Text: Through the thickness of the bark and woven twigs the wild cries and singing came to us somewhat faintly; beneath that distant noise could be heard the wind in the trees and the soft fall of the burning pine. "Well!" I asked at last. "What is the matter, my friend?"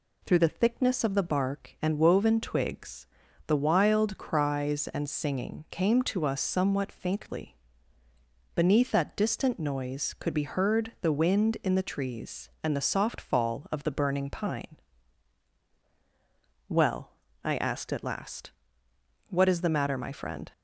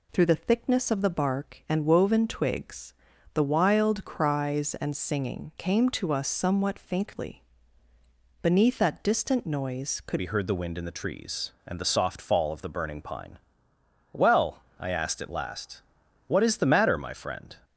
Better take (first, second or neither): first